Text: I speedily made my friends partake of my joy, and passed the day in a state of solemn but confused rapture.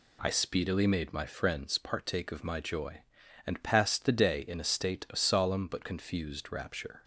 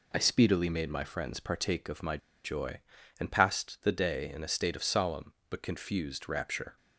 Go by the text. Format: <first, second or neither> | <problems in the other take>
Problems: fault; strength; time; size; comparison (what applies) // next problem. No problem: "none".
first | pauses between "my" and "joy"; slight; at 2.1 s; 0.26 s long